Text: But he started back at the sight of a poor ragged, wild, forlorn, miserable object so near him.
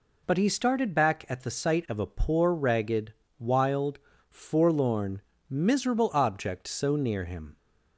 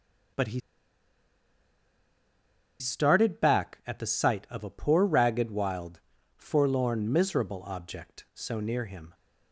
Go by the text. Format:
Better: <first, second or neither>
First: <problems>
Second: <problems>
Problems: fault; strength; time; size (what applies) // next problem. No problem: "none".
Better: first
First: none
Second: starts louder than the rest; strong; until 3.5 s; 8 dB // pauses between "he" and "started"; strong; at 0.5 s; 2.2 s long